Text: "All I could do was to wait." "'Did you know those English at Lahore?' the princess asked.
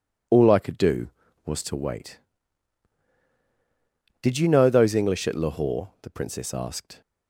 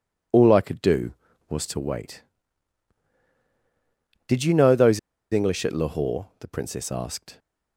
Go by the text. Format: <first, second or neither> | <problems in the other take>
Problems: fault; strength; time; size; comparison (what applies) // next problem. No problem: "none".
first | pauses between "those" and "English"; slight; at 4.9 s; 0.32 s long